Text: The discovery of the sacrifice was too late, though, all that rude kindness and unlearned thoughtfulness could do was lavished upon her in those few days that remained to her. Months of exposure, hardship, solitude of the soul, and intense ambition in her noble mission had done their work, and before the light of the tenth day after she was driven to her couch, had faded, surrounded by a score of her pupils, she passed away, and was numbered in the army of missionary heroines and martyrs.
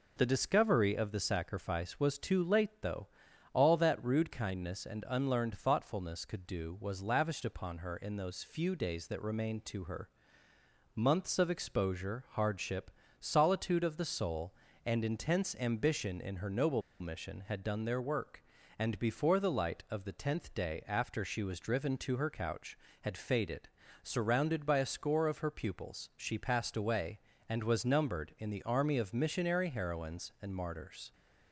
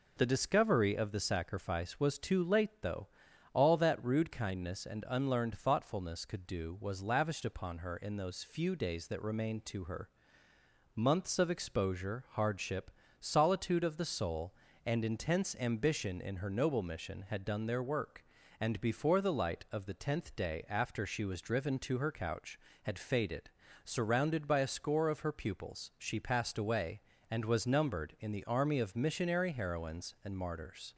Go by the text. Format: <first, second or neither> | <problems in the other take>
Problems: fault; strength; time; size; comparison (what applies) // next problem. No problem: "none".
second | pauses between "noble" and "mission"; slight; at 16.8 s; 0.18 s long